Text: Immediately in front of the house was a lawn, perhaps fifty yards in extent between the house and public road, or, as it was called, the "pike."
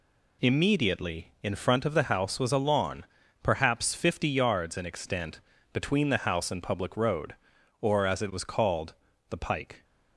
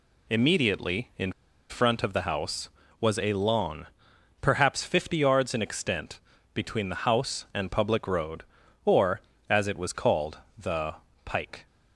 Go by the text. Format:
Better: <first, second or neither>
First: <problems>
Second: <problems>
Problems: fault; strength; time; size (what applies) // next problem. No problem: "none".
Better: first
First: pauses between "extent" and "between"; slight; at 5.3 s; 0.34 s long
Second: pauses between "in" and "front"; at 1.3 s; 0.38 s long // pauses between "extent" and "between"; slight; at 6.1 s; 0.34 s long // pauses between "the" and "pike"; slight; at 10.9 s; 0.30 s long